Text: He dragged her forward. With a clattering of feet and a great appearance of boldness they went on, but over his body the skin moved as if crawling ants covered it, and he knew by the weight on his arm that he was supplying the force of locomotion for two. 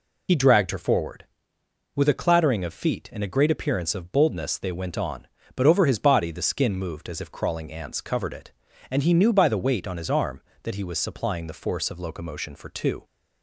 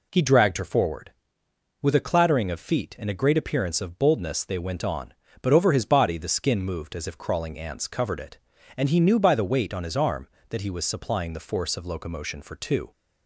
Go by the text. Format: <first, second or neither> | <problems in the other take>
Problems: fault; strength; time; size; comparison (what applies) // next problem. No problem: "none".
second | loses the start of "He"; at 0.2 s; 45 ms